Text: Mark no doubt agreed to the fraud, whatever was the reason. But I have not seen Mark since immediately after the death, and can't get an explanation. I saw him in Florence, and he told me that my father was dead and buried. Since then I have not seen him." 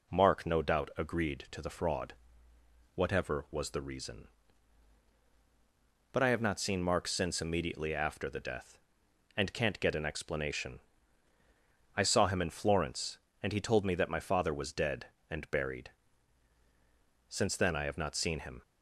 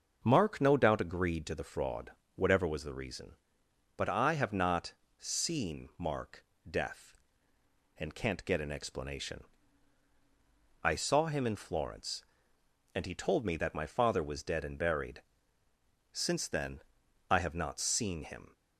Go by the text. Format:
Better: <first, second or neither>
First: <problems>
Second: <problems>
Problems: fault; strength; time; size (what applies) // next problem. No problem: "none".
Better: first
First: none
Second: starts louder than the rest; until 1.2 s; 6.5 dB // pauses between "not" and "seen"; slight; at 4.9 s; 0.26 s long // skips "since immediately after the"; at 6.5 s // pauses between "then" and "I"; noticeable; at 16.8 s; 0.48 s long